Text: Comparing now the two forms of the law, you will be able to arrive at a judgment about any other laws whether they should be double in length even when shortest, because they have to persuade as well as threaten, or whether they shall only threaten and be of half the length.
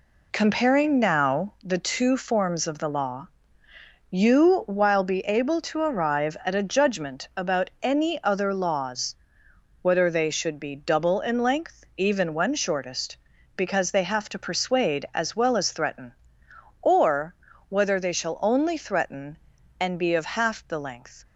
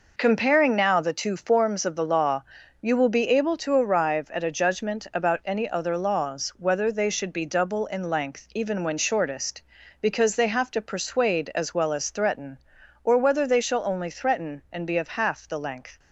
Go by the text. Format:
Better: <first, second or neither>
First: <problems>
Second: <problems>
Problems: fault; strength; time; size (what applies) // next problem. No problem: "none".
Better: second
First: says "while" for "will"; at 4.6 s // pauses between "laws" and "whether"; noticeable; at 9.1 s; 0.66 s long // pauses between "or" and "whether"; slight; at 17.3 s; 0.34 s long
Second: none